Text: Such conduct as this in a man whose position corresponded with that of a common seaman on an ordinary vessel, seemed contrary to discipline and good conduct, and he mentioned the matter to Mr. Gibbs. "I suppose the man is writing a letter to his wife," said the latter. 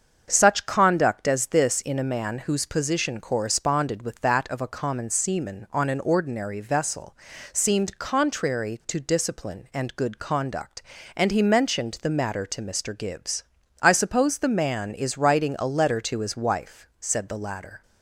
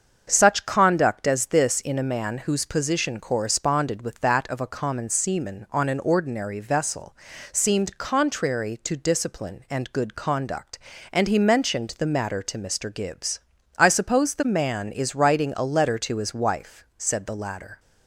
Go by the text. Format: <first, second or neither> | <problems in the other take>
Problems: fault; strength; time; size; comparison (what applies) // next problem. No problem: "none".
neither | starts louder than the rest; the same in both